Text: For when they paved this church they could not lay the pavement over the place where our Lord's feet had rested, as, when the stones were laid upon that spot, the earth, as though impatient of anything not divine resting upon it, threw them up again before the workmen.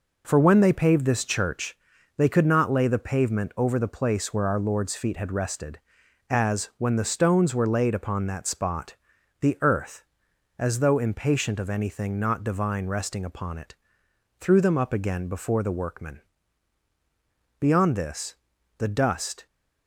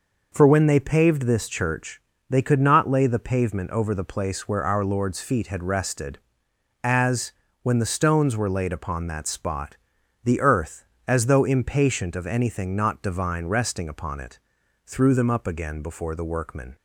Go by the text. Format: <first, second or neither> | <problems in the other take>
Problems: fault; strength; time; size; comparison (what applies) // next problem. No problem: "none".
second | pauses between "church" and "they"; at 1.7 s; 0.38 s long; slight in the second // goes on to say "Beyond this the dust"; strong; from 17.5 s on; 1.8 s long